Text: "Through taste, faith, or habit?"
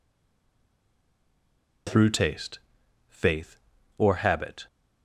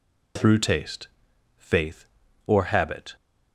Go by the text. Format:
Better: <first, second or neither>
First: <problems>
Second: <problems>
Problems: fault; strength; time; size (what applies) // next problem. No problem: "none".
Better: second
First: stays silent before the first word; noticeable; until 1.8 s; 1.8 s long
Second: none